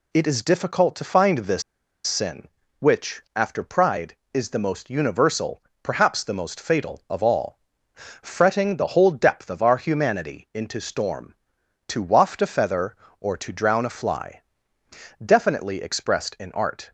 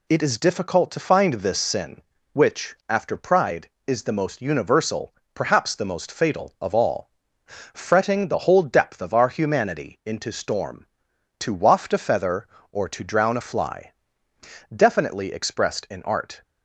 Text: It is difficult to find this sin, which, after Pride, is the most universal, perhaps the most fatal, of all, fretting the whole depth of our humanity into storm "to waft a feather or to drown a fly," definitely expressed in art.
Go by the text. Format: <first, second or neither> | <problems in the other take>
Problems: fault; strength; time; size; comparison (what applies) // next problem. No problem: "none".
second | pauses between "this" and "sin"; at 1.6 s; 0.43 s long